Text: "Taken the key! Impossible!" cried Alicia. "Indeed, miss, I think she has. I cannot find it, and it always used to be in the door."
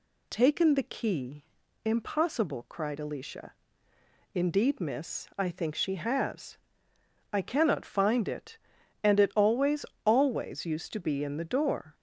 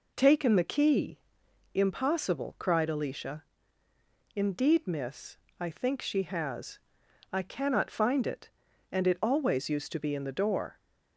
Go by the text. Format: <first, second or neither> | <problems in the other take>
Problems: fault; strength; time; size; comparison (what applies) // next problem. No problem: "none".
second | says "always" twice; at 10.0 s